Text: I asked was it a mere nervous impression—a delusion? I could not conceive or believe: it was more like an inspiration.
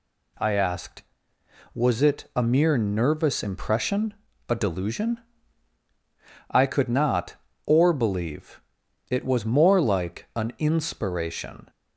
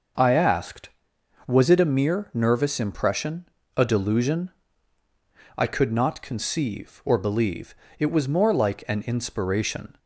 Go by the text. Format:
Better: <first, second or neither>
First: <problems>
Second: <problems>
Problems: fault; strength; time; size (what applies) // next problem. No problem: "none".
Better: second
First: skips "conceive"; at 7.5 s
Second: none